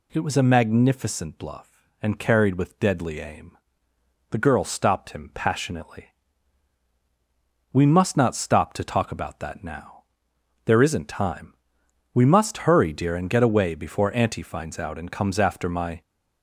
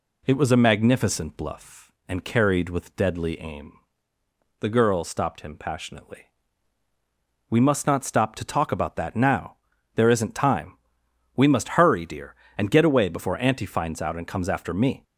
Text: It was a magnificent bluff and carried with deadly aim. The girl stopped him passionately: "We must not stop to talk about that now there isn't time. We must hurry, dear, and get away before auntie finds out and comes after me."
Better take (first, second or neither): second